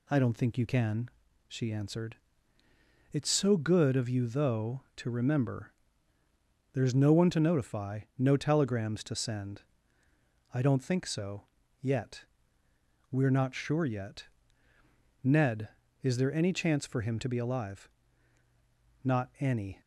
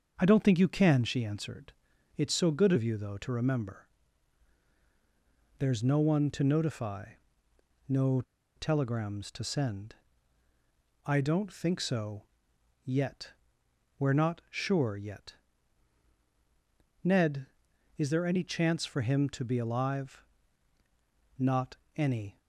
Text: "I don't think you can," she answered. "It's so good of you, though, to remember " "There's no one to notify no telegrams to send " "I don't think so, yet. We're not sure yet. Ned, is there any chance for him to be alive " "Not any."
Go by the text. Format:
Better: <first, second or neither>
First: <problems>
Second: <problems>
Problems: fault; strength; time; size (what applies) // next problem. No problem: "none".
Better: first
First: pauses between "notify" and "no"; slight; at 8.0 s; 0.16 s long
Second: starts louder than the rest; strong; until 1.1 s; 7.5 dB // pauses between "notify" and "no"; noticeable; at 7.1 s; 0.74 s long // pauses between "no" and "telegrams"; slight; at 8.2 s; 0.33 s long // pauses between "Not" and "any"; slight; at 21.7 s; 0.22 s long